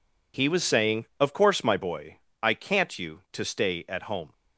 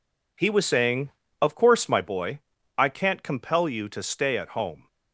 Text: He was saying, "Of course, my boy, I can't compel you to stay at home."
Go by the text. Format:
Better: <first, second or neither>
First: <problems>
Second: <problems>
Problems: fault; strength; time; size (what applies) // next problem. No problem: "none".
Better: second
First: skips "compel"; at 2.9 s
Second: none